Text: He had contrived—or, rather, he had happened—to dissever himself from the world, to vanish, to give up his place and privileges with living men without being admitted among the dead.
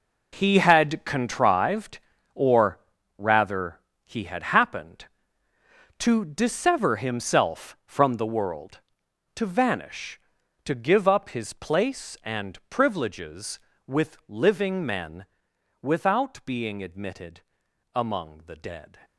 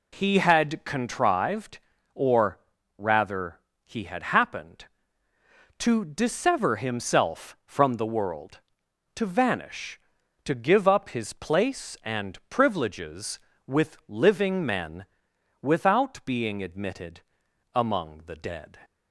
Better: second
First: gets quieter; strong; throughout; 11.5 dB // pauses between "men" and "without"; noticeable; at 15.2 s; 0.58 s long // pauses between "admitted" and "among"; noticeable; at 17.4 s; 0.52 s long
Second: pauses between "men" and "without"; noticeable; at 15.0 s; 0.58 s long // pauses between "admitted" and "among"; noticeable; at 17.2 s; 0.52 s long

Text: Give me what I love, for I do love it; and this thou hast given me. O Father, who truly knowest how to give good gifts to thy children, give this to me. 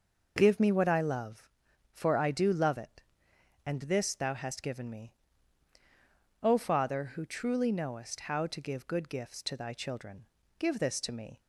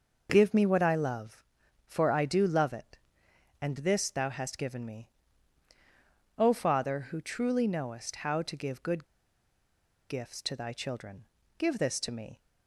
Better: first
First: none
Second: pauses between "good" and "gifts"; at 9.0 s; 1.0 s long

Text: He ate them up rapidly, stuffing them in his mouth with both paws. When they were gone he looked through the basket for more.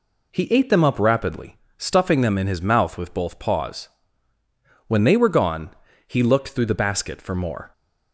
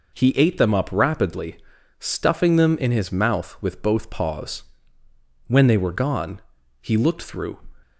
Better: first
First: pauses between "gone" and "he"; slight; at 5.6 s; 0.36 s long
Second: pauses between "gone" and "he"; at 6.4 s; 0.40 s long // stops before "the basket for more"; at 7.8 s

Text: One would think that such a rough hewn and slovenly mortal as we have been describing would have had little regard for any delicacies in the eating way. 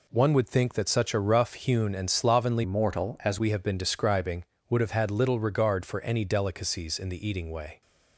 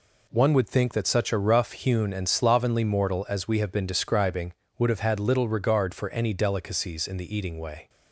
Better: second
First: changes voice from "mortal" to "as"; from 2.6 to 3.3 s; 0.7 s long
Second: none

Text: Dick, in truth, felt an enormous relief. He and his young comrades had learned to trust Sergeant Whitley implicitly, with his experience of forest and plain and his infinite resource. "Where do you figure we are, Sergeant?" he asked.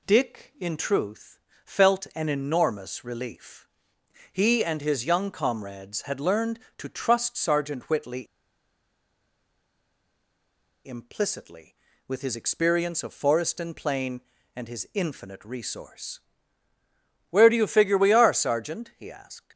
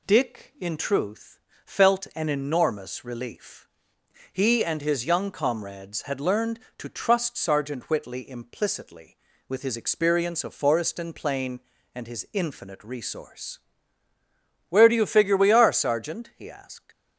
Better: second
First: pauses between "Whitley" and "implicitly"; strong; at 8.2 s; 2.6 s long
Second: none

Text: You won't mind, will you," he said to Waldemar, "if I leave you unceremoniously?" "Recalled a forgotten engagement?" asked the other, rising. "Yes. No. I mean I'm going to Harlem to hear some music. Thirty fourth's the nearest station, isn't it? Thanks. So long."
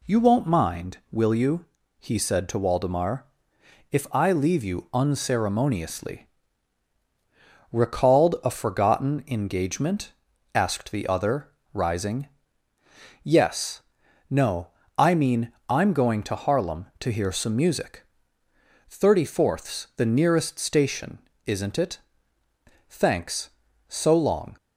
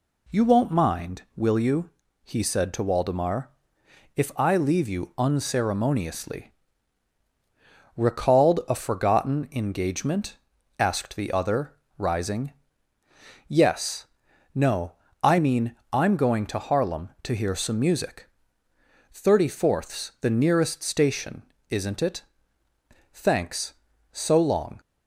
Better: neither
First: pauses between "mean" and "I'm"; slight; at 15.5 s; 0.18 s long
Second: pauses between "mean" and "I'm"; slight; at 15.7 s; 0.18 s long

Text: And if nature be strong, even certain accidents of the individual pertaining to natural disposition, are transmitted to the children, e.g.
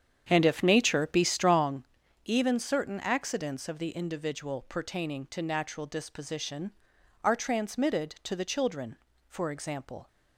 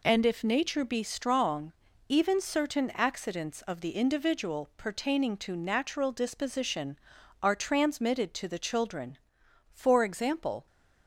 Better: second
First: starts louder than the rest; strong; until 1.7 s; 8.5 dB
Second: none

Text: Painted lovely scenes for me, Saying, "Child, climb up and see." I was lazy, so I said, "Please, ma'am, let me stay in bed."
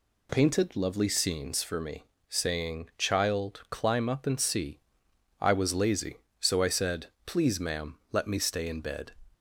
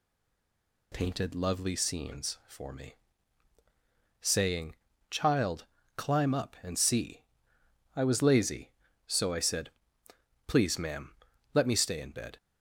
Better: first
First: none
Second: stays silent before the first word; slight; until 0.9 s; 0.9 s long

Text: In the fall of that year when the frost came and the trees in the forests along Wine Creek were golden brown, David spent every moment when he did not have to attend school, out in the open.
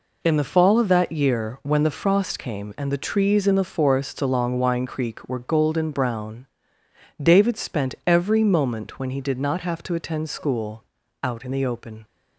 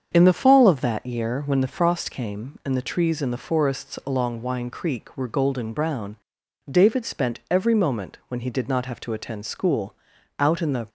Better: first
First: none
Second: starts louder than the rest; strong; until 1.1 s; 7.5 dB // stops before "open"; at 10.8 s

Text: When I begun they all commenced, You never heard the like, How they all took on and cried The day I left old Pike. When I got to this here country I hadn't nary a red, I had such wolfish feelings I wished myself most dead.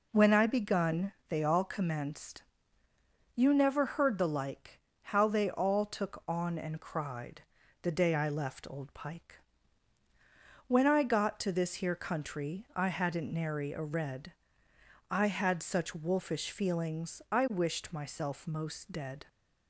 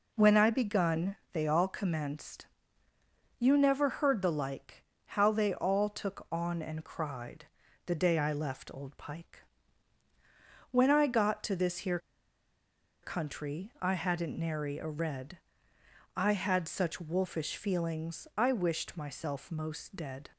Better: first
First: pauses between "begun" and "they"; slight; at 1.1 s; 0.18 s long // pauses between "cried" and "The"; at 7.4 s; 0.40 s long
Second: pauses between "begun" and "they"; slight; at 1.1 s; 0.18 s long // pauses between "cried" and "The"; at 7.4 s; 0.40 s long // pauses between "here" and "country"; at 11.9 s; 1.0 s long

